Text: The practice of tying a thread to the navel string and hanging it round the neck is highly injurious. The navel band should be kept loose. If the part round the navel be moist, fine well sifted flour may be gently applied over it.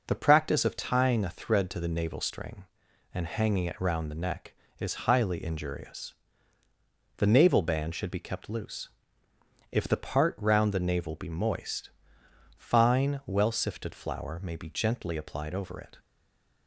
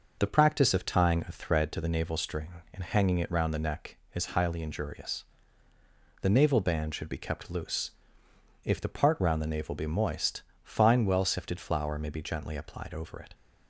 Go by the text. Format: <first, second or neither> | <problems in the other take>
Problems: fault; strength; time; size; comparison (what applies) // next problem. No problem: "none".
second | stays silent after the last word; slight; from 15.9 s on; 0.7 s long